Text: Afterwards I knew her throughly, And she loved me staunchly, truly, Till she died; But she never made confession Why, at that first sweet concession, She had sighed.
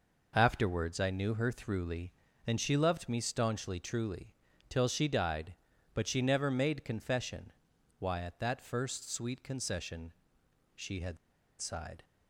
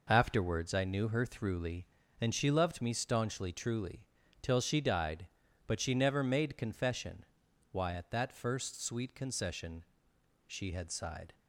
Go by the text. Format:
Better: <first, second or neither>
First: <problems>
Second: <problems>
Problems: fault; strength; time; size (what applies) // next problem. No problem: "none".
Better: second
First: pauses between "confession" and "Why"; noticeable; at 7.5 s; 0.48 s long // pauses between "had" and "sighed"; at 11.1 s; 0.44 s long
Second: pauses between "confession" and "Why"; noticeable; at 7.2 s; 0.48 s long